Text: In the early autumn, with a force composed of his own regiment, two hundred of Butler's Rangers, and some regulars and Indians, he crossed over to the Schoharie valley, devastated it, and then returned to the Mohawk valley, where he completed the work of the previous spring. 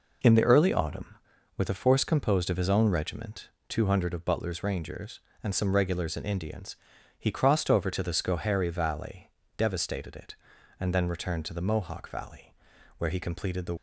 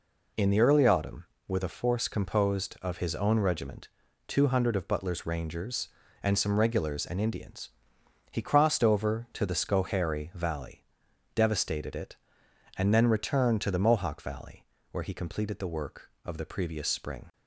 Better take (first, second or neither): second